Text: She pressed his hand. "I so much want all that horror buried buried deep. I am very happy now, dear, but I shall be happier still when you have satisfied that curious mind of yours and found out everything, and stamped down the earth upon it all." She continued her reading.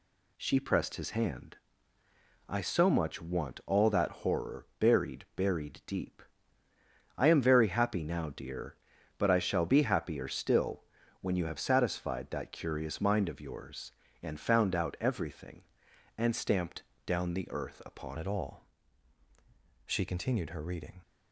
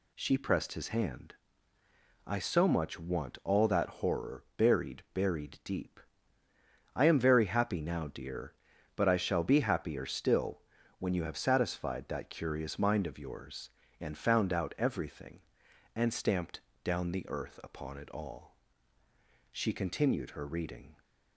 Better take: second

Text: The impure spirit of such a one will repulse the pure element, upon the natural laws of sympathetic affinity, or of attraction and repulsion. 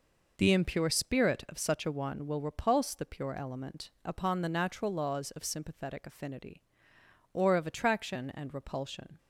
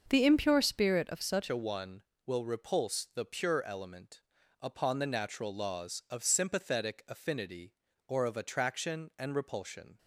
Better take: first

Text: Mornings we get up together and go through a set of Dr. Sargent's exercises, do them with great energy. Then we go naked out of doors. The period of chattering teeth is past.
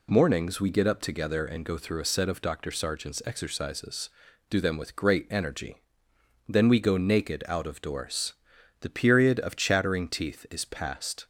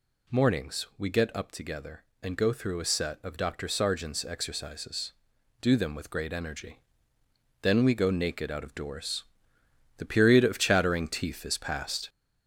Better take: first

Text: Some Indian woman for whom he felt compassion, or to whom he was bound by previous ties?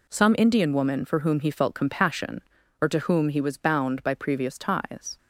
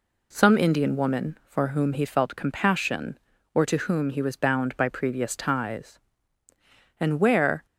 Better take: first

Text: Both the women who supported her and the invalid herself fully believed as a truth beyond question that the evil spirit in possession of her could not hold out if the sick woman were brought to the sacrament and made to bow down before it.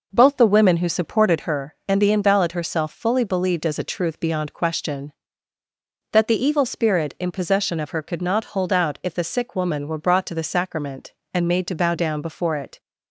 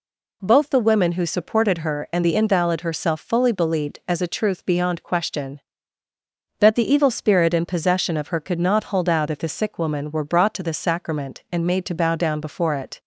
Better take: second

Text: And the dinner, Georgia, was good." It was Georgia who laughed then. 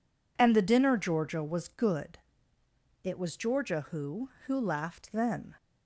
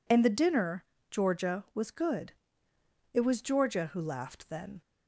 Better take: second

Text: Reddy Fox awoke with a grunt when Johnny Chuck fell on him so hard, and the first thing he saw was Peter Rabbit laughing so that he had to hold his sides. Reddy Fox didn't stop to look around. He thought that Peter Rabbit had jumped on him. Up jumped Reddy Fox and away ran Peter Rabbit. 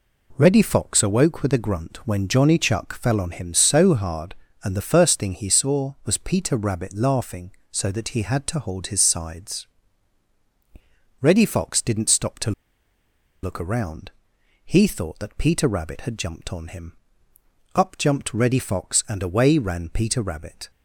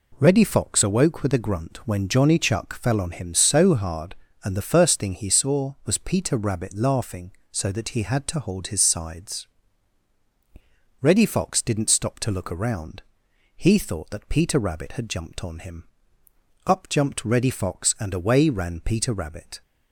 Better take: second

